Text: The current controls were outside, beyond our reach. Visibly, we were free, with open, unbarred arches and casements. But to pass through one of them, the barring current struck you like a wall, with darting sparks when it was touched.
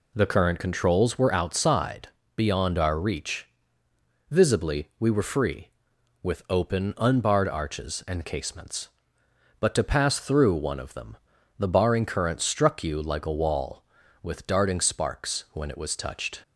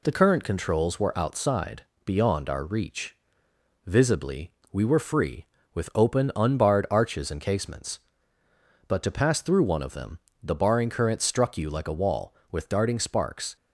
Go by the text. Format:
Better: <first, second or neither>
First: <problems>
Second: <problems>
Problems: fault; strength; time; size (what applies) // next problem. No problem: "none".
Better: first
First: none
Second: stops before "when it was touched"; at 13.5 s